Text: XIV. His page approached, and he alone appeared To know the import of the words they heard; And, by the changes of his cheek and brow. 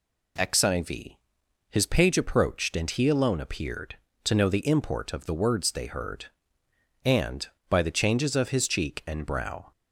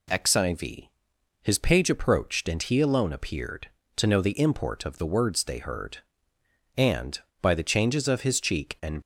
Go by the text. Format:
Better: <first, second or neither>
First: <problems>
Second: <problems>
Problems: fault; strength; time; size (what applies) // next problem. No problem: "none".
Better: first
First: none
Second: stops before "brow"; at 9.0 s